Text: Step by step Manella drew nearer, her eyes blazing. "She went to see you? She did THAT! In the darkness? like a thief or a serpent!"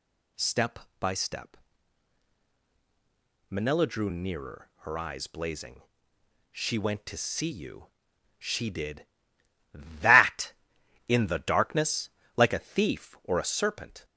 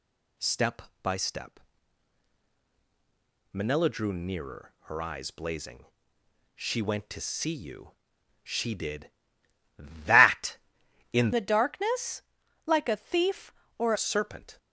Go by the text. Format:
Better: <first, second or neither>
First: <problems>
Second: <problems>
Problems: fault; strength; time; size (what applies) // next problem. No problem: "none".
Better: first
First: pauses between "step" and "Manella"; strong; at 1.5 s; 1.9 s long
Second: pauses between "step" and "Manella"; strong; at 1.5 s; 1.9 s long // changes voice from "the" to "or"; from 11.3 to 13.9 s; 2.6 s long